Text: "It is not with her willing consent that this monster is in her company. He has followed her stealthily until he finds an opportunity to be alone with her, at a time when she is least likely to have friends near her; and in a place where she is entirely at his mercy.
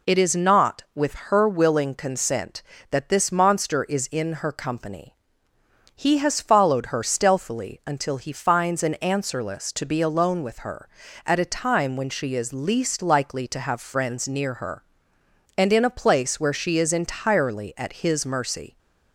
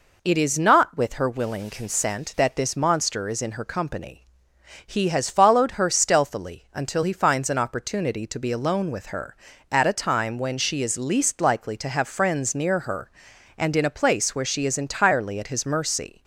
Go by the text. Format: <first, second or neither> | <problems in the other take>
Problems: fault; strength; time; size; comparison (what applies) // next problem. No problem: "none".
second | says "answerless" for "opportunity"; at 9.0 s